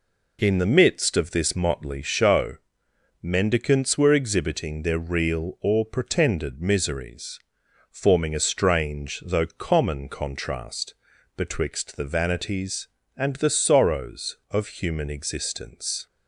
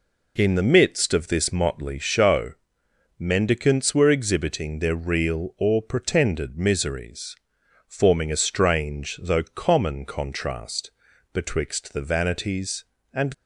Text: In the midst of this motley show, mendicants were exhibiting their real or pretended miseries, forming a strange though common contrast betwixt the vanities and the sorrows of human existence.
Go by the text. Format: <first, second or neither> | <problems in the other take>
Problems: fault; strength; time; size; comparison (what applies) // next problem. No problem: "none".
first | pauses between "contrast" and "betwixt"; at 10.9 s; 0.42 s long; also in the first // stops before "the sorrows of human existence"; at 13.3 s